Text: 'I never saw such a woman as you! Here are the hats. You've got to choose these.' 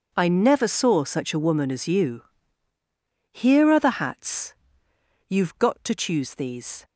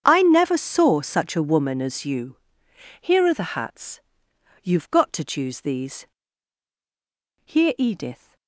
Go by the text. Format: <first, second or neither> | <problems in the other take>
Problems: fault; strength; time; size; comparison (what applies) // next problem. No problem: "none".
first | starts louder than the rest; strong; until 1.0 s; 8 dB // goes on to say "Here Edith"; noticeable; from 7.4 s on; 0.90 s long